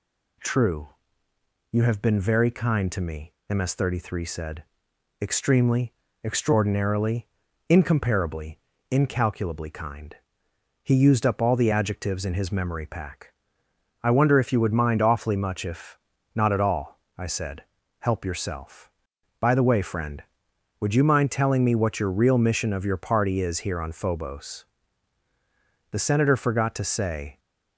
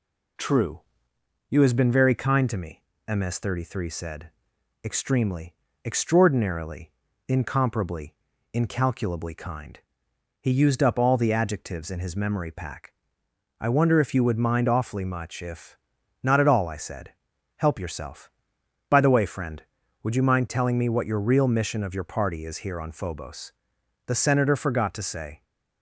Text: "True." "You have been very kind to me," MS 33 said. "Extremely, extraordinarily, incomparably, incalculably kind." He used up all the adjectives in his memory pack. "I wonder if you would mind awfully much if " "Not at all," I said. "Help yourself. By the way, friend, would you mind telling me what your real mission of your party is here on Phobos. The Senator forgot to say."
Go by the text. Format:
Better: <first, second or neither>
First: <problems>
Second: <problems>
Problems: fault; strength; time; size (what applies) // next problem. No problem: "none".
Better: first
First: none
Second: says "has" for "have"; at 1.6 s